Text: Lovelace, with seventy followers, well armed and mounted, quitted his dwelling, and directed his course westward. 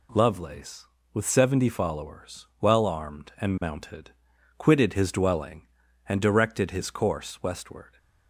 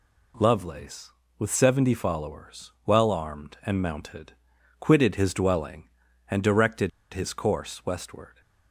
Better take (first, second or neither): first